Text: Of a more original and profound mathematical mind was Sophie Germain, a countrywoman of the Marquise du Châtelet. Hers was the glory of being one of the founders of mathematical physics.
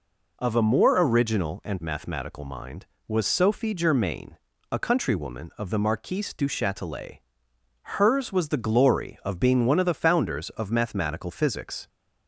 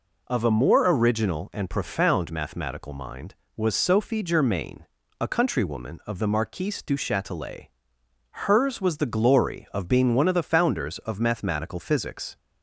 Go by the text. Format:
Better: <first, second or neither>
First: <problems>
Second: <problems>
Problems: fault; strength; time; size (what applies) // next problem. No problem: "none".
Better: second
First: skips "profound"; at 1.8 s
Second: none